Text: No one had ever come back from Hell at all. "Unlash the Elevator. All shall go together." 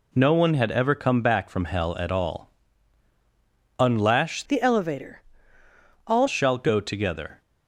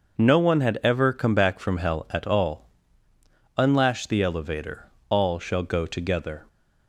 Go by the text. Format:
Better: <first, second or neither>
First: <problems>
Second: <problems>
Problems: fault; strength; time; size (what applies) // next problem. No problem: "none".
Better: second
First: changes voice from "the" to "All"; from 4.4 to 6.2 s; 1.8 s long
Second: none